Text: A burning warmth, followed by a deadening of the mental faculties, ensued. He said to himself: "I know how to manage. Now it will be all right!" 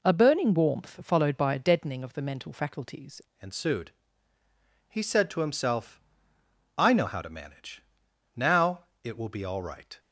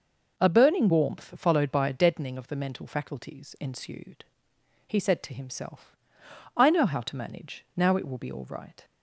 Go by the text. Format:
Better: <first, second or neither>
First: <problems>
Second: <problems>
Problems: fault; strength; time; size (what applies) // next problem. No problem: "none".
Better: second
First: changes voice at "ensued"; from 3.4 s on; 6.5 s long // pauses between "Now" and "it"; slight; at 8.8 s; 0.20 s long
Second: none